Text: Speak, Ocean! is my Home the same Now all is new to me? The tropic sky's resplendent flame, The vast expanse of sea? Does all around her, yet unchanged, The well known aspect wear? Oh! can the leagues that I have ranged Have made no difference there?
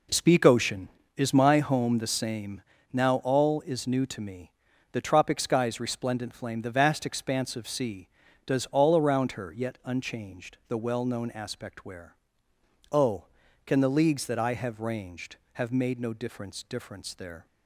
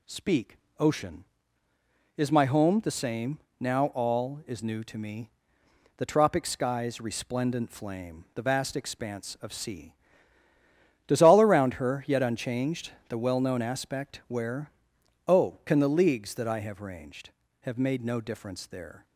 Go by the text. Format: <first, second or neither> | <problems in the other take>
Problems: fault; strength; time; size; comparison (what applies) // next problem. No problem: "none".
second | pauses between "same" and "Now"; slight; at 2.6 s; 0.30 s long; slight in the second // says "difference" twice; at 16.6 s